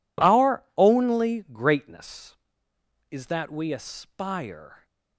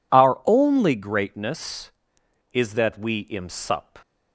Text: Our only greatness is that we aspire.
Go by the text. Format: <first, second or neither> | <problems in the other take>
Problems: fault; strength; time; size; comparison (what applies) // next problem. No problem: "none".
first | says "imsup" for "aspire"; at 3.2 s